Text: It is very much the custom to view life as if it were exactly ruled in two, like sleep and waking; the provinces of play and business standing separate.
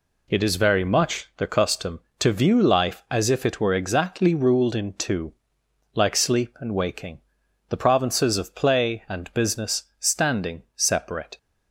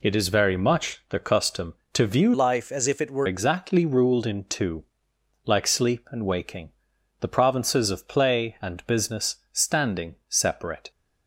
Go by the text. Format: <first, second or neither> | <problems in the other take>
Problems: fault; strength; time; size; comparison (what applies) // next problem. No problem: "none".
first | changes voice from "life" to "were"; from 2.3 to 3.2 s; 0.9 s long // pauses between "business" and "standing"; slight; at 9.3 s; 0.16 s long; slight in the first